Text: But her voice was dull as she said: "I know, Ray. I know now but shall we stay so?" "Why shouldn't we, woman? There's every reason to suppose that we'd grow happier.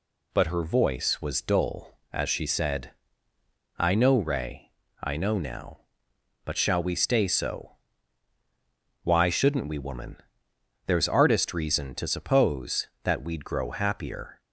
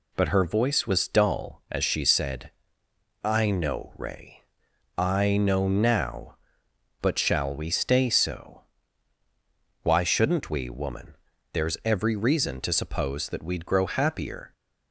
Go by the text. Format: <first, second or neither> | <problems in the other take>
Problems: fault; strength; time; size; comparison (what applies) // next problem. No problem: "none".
second | says "artist" for "every"; at 11.0 s